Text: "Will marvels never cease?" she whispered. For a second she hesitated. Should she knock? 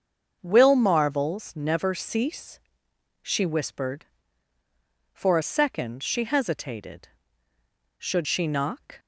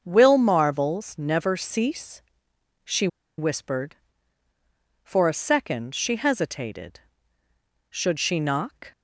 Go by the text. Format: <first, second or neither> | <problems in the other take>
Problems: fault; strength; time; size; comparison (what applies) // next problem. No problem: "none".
first | starts louder than the rest; until 1.0 s; 6.5 dB; also in the first // pauses between "she" and "whispered"; slight; at 3.0 s; 0.30 s long